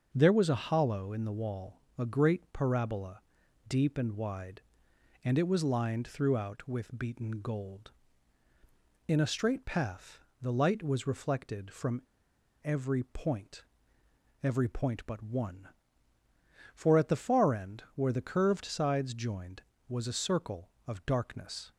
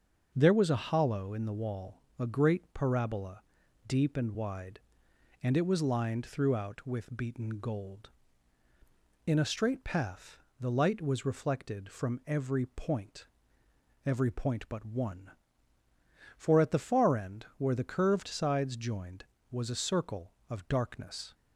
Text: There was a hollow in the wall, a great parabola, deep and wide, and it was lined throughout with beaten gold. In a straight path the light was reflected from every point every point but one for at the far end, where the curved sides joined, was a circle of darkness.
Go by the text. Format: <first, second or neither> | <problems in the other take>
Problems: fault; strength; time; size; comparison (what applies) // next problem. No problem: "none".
second | starts louder than the rest; until 1.1 s; 6 dB; also in the second // pauses between "path" and "the"; slight; at 10.1 s; 0.24 s long; slight in the second // pauses between "from" and "every"; noticeable; at 12.0 s; 0.62 s long // pauses between "point" and "every"; noticeable; at 13.6 s; 0.80 s long; noticeable in the second